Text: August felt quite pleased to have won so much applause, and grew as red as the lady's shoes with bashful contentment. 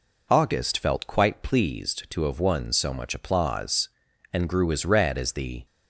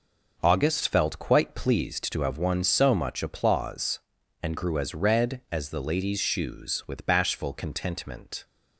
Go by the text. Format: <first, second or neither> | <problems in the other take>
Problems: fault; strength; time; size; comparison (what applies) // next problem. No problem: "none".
second | stops before "lady's shoes with bashful contentment"; at 5.6 s